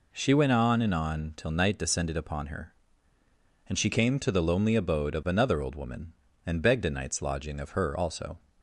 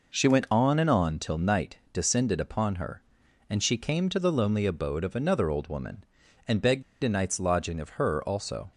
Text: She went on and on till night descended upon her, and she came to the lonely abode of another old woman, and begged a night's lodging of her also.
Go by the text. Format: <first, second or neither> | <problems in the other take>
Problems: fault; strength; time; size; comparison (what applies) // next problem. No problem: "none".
first | pauses between "begged" and "a"; slight; at 6.8 s; 0.20 s long